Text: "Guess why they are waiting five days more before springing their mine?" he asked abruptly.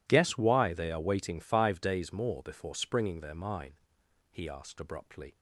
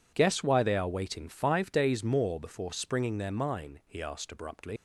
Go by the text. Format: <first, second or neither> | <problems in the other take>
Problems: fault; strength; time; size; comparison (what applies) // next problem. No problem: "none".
first | leaves "abruptly" unfinished; at 4.7 s; 85 ms